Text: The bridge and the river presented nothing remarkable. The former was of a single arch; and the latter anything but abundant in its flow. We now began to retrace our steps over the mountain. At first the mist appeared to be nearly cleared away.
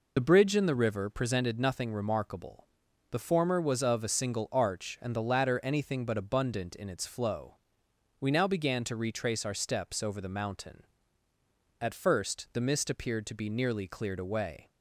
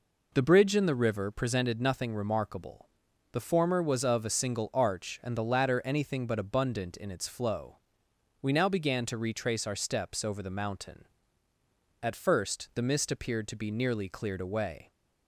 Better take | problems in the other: second | loses the start of "The"; at 0.1 s; 40 ms

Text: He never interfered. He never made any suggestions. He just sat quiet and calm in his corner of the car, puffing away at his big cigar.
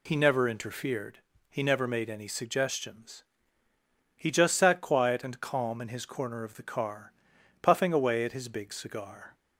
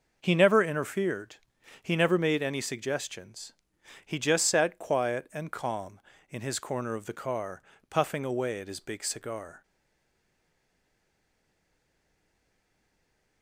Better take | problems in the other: first | stays silent after the last word; strong; from 9.6 s on; 3.8 s long

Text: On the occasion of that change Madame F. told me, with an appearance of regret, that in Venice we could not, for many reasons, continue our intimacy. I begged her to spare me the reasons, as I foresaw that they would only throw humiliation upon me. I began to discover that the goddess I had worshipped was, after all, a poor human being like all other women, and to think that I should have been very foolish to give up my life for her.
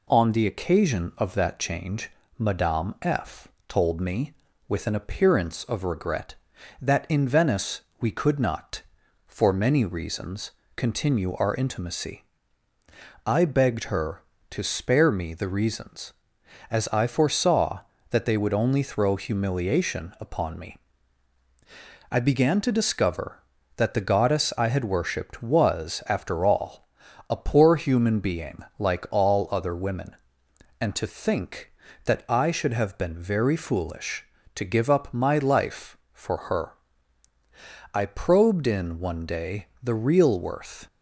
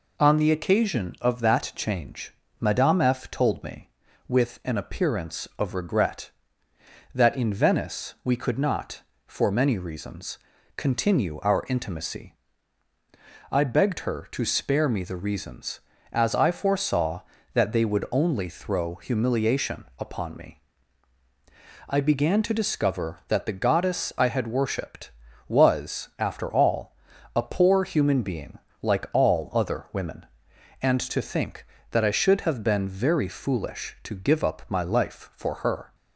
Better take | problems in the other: second | pauses between "change" and "Madame"; slight; at 2.0 s; 0.30 s long; slight in the second // pauses between "F" and "told"; slight; at 3.4 s; 0.18 s long // pauses between "Venice" and "we"; slight; at 7.8 s; 0.20 s long // pauses between "being" and "like"; slight; at 28.6 s; 0.16 s long; slight in the second // goes on to say "I probed in one day the real worth"; strong; from 37.9 s on; 2.9 s long

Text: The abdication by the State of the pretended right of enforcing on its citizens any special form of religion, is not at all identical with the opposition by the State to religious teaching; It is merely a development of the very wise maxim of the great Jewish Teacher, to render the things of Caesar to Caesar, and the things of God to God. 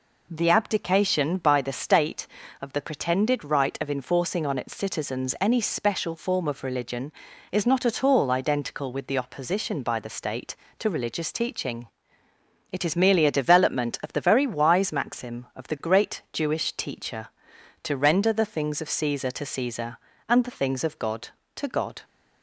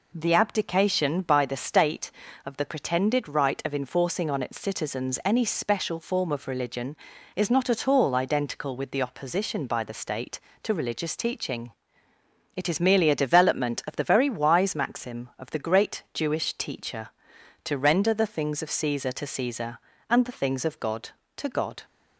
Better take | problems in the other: neither | none

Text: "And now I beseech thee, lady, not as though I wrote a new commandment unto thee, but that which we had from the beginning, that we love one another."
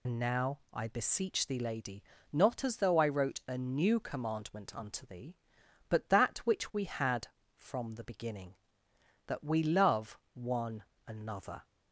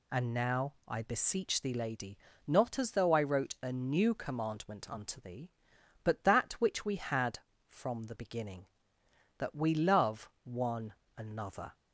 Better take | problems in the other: second | loses the start of "And"; at 0.0 s; 85 ms // pauses between "love" and "one"; slight; at 10.1 s; 0.18 s long; slight in the second // pauses between "one" and "another"; slight; at 10.8 s; 0.24 s long; slight in the second

